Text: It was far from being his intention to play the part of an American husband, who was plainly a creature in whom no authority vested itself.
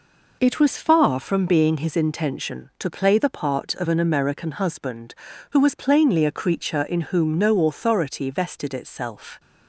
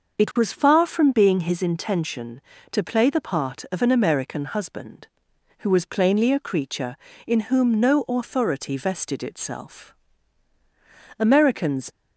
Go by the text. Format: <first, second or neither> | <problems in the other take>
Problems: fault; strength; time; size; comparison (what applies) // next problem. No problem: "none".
first | starts louder than the rest; until 1.2 s; 6 dB // goes on to say "Americans"; noticeable; from 11.1 s on; 0.72 s long